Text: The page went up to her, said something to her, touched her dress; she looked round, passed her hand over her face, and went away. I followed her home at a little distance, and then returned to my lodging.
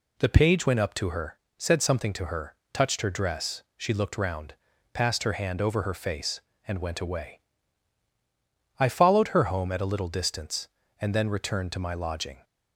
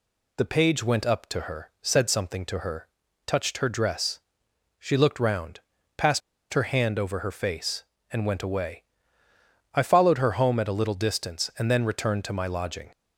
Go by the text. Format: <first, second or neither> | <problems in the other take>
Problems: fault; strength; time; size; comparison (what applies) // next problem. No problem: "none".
first | pauses between "passed" and "her"; slight; at 6.2 s; 0.32 s long